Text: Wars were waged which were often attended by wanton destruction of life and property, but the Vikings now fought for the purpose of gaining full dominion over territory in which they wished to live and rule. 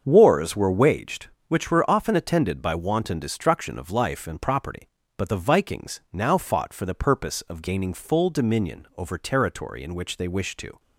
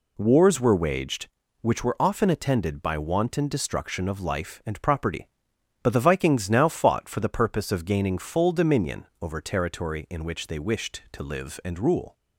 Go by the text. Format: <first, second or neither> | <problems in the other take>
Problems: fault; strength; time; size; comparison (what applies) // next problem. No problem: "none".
second | starts louder than the rest; until 1.0 s; 7 dB // stops before "live and rule"; at 10.7 s